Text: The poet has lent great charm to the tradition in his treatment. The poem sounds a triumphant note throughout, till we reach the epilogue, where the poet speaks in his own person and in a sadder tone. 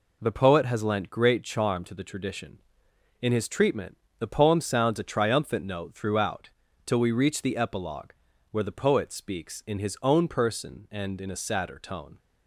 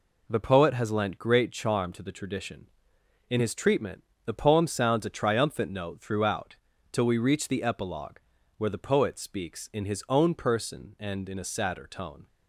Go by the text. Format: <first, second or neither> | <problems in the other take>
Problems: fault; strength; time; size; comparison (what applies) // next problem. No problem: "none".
neither | none